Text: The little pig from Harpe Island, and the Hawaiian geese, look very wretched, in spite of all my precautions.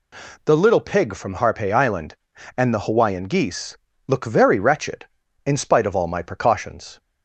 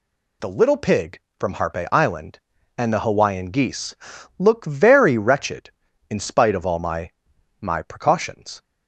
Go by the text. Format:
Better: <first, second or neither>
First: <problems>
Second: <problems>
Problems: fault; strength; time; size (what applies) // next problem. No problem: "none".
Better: first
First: none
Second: says "my" twice; at 7.5 s